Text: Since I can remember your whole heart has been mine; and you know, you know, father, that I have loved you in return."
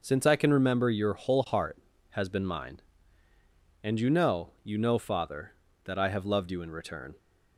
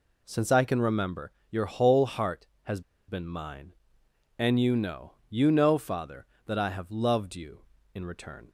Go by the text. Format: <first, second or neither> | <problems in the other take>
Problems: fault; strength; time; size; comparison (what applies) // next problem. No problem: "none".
first | pauses between "remember" and "your"; slight; at 1.3 s; 0.18 s long // pauses between "has" and "been"; slight; at 2.8 s; 0.27 s long